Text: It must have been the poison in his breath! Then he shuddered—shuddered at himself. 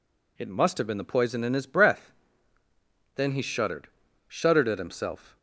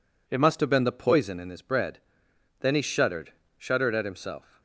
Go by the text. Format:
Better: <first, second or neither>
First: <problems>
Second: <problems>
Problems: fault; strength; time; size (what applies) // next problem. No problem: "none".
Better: first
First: none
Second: says "bread" for "breath"; at 1.6 s